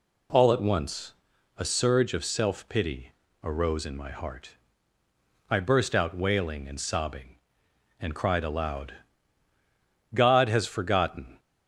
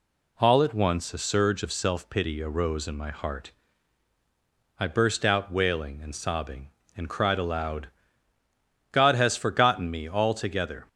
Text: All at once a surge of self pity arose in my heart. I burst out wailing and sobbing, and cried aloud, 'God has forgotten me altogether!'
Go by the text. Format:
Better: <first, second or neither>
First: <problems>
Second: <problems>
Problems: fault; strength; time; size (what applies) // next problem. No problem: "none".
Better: second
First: pauses between "once" and "a"; noticeable; at 1.1 s; 0.46 s long // pauses between "pity" and "arose"; slight; at 3.1 s; 0.32 s long // stops before "me altogether"; at 11.3 s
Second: none